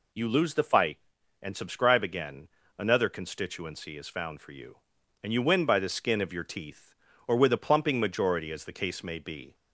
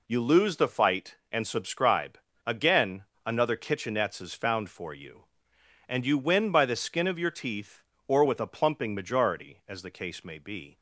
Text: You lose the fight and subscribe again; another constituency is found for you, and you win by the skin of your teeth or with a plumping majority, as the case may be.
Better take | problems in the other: first | pauses between "subscribe" and "again"; slight; at 2.1 s; 0.26 s long // says "kitchenettes" for "constituency"; at 3.5 s

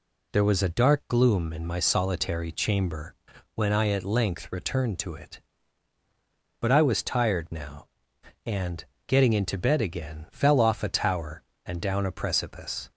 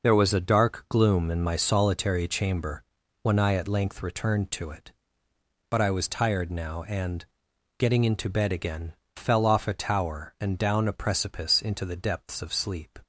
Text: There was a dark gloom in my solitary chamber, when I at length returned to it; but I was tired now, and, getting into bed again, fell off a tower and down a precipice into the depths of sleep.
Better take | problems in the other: second | stops before "into the depths of sleep"; at 12.9 s

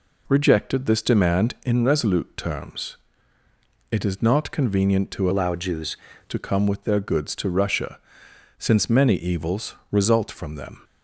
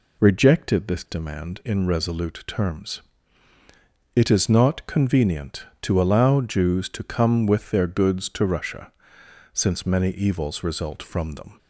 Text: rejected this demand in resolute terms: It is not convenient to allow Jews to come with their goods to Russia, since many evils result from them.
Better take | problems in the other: second | changes voice from "allow" to "Jews"; from 5.3 to 5.9 s; 0.6 s long // pauses between "evils" and "result"; slight; at 9.7 s; 0.16 s long

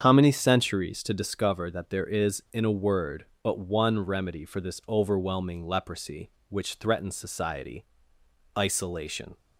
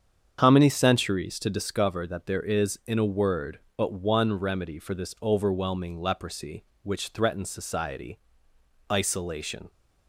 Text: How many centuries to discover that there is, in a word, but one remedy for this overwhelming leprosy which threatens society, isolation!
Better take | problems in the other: neither | starts louder than the rest; strong; the same in both

